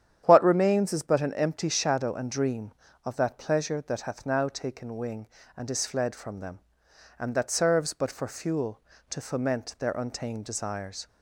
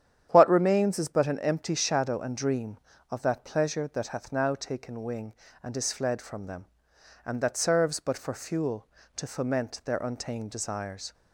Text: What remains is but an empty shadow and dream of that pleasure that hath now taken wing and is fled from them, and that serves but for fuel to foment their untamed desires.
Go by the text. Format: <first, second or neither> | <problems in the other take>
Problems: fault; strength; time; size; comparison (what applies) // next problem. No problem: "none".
neither | starts louder than the rest; strong; the same in both